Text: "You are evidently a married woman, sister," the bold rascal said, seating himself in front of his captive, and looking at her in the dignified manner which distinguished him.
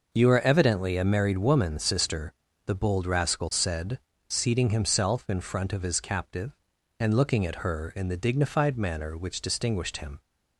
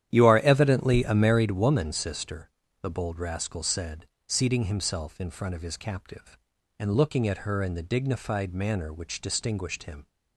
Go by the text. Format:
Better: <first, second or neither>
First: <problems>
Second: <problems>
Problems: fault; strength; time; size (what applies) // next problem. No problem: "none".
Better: first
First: none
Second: starts louder than the rest; strong; until 1.6 s; 11 dB